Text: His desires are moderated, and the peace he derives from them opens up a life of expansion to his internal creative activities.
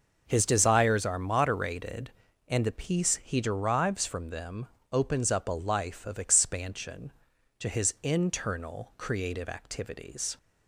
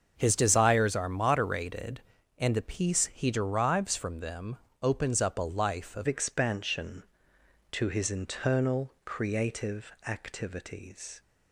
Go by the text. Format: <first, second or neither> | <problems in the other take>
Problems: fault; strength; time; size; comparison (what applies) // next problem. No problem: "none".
first | starts louder than the rest; until 1.1 s; 6.5 dB; noticeable in the first // pauses between "them" and "opens"; slight; at 4.5 s; 0.24 s long; slight in the first // changes voice at "expansion"; from 6.0 s on; 5.2 s long // pauses between "creative" and "activities"; slight; at 9.9 s; 0.16 s long